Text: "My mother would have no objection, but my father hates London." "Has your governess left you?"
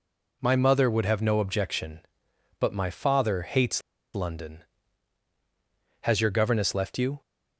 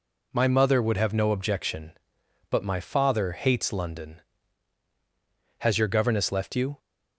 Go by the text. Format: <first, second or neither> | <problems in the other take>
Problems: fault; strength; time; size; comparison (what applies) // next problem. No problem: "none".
second | pauses between "hates" and "London"; slight; at 3.8 s; 0.35 s long